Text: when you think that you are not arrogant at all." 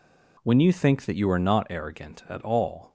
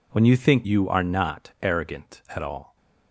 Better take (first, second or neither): first